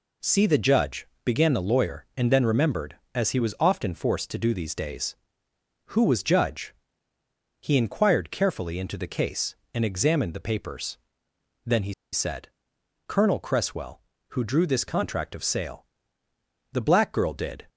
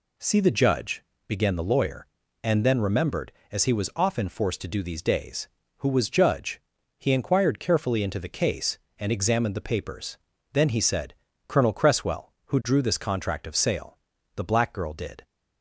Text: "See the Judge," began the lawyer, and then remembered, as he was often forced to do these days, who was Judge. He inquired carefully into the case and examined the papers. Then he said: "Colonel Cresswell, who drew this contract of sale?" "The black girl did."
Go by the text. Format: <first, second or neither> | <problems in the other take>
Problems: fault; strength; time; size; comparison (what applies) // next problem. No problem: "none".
second | pauses between "he" and "said"; slight; at 11.9 s; 0.19 s long